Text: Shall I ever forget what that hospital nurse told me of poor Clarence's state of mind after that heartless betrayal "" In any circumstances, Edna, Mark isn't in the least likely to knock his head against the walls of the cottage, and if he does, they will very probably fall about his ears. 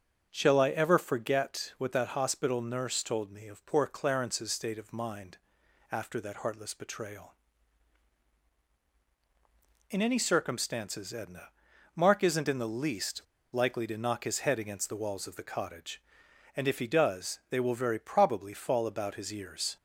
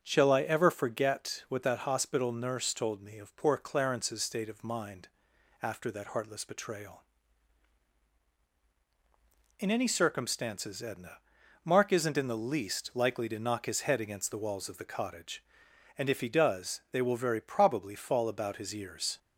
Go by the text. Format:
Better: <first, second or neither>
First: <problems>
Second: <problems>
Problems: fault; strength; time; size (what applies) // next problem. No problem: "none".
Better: second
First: starts louder than the rest; strong; until 1.3 s; 9.5 dB // pauses between "mind" and "after"; noticeable; at 5.3 s; 0.54 s long // pauses between "least" and "likely"; slight; at 13.2 s; 0.29 s long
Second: starts louder than the rest; strong; until 1.0 s; 9.5 dB // pauses between "mind" and "after"; noticeable; at 5.0 s; 0.54 s long